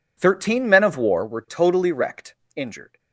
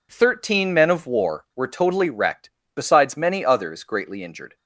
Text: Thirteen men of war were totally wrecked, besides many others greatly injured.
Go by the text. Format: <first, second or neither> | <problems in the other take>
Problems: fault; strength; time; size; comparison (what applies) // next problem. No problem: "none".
second | skips "besides many others greatly"; at 2.4 s